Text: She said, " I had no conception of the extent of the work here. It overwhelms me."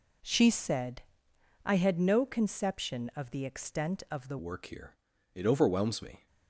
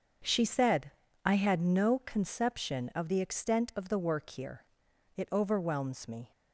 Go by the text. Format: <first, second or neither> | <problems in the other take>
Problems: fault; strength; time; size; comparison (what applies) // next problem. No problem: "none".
second | changes voice at "work"; from 4.3 s on; 1.9 s long